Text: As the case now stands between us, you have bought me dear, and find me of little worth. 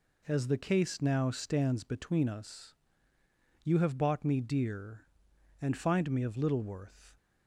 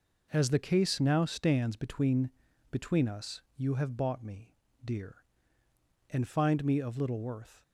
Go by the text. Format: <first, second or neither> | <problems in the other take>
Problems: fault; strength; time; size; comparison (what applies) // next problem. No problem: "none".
first | says "between" twice; at 2.7 s // pauses between "me" and "dear"; slight; at 4.5 s; 0.32 s long